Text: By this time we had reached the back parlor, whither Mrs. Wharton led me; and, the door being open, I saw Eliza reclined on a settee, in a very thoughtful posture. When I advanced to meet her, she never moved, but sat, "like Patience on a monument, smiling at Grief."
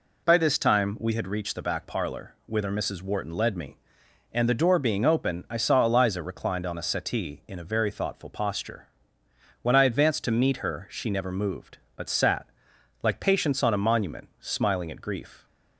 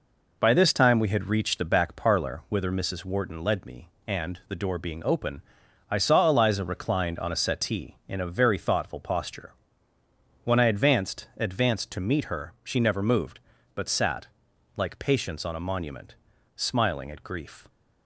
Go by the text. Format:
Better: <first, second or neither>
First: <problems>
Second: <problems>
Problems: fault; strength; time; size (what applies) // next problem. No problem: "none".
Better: first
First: none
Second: says "advanced" twice; at 11.3 s